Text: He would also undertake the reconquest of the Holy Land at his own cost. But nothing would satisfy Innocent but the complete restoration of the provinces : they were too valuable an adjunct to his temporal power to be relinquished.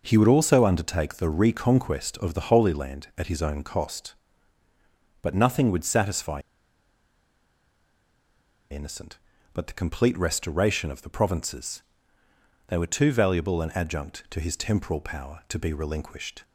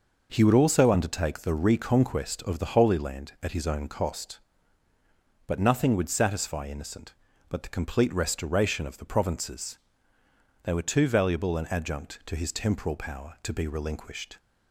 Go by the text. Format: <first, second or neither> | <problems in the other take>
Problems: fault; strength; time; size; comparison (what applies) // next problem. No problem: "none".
second | pauses between "satisfy" and "Innocent"; strong; at 6.4 s; 2.3 s long